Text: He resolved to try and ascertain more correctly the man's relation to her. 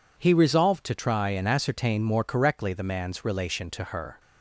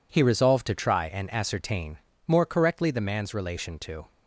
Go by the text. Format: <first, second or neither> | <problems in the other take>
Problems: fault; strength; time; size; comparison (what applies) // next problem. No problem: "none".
first | pauses between "ascertain" and "more"; slight; at 1.9 s; 0.28 s long // stops before "her"; at 4.1 s